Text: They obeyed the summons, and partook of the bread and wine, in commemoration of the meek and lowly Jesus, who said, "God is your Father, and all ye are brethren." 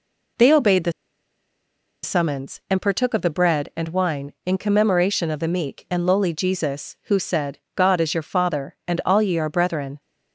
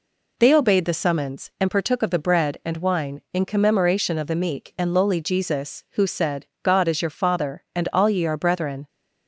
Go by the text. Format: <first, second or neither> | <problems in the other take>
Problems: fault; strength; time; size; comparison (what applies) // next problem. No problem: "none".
second | pauses between "the" and "summons"; at 0.9 s; 1.1 s long